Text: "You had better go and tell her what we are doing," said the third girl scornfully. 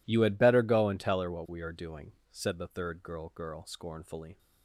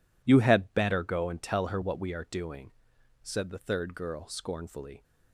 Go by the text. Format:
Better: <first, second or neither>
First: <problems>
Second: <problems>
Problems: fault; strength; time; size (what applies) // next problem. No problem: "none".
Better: second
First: says "girl" twice; at 3.3 s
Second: none